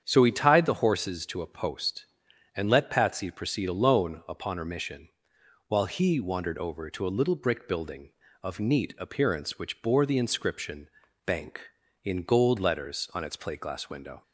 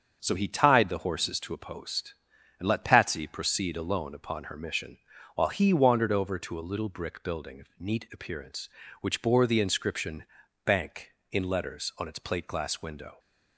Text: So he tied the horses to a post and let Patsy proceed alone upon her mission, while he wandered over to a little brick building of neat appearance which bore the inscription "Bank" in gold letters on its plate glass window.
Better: first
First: starts louder than the rest; strong; until 1.0 s; 8 dB // pauses between "inscription" and "Bank"; slight; at 10.8 s; 0.36 s long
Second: starts louder than the rest; until 1.2 s; 6.5 dB // pauses between "inscription" and "Bank"; at 10.2 s; 0.40 s long // skips "gold"; at 11.4 s

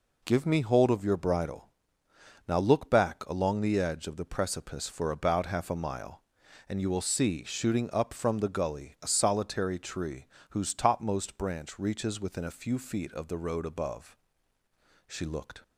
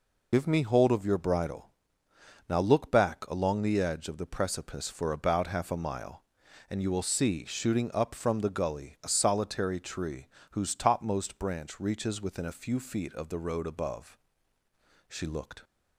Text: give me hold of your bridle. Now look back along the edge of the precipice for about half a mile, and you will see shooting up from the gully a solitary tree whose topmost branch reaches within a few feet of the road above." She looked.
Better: first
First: pauses between "tree" and "whose"; slight; at 10.2 s; 0.24 s long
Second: loses the start of "give"; at 0.3 s; 75 ms // pauses between "tree" and "whose"; slight; at 10.2 s; 0.24 s long

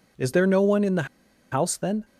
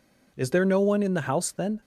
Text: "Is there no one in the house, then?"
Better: second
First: pauses between "the" and "house"; noticeable; at 1.0 s; 0.47 s long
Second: none

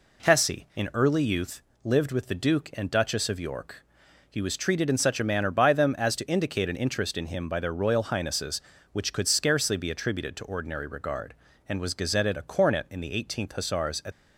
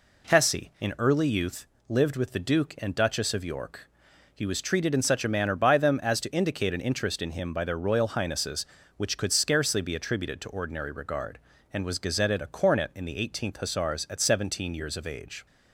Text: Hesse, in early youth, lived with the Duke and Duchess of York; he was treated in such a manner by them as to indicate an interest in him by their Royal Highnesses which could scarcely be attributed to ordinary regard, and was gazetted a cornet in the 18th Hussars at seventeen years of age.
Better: second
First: stops before "seventeen years of age"; at 14.1 s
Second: none

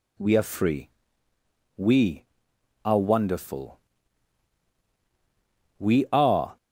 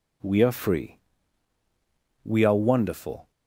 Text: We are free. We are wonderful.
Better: second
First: goes on to say "We are"; noticeable; from 5.7 s on; 0.78 s long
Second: none

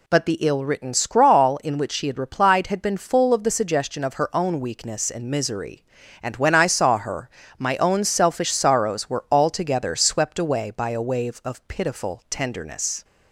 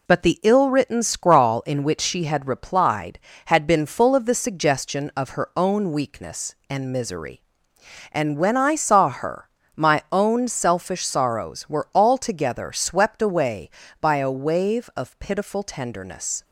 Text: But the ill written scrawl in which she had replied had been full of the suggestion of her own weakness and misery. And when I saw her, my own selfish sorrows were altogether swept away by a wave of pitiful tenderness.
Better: neither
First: none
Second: none

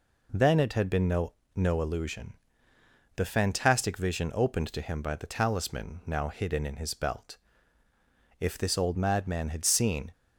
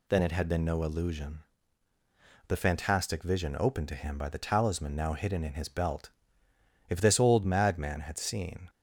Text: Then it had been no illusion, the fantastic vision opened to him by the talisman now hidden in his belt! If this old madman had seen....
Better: second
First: says "no" twice; at 1.5 s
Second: none

